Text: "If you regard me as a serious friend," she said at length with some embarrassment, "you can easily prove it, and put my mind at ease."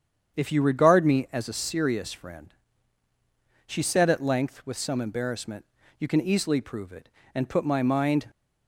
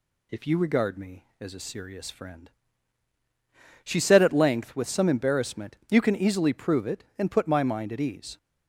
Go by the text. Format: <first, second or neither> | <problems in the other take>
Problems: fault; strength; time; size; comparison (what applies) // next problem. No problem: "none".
second | starts louder than the rest; strong; until 1.4 s; 8 dB // stops before "at ease"; at 8.2 s